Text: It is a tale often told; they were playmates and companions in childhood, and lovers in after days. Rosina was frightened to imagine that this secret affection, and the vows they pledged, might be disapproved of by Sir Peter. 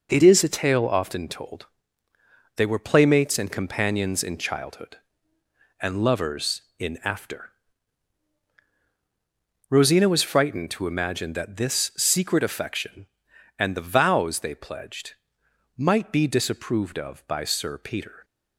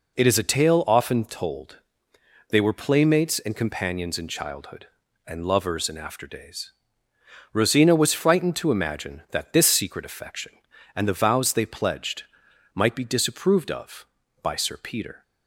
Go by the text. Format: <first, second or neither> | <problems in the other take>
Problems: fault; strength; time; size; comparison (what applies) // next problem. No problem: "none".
second | skips "days"; at 8.5 s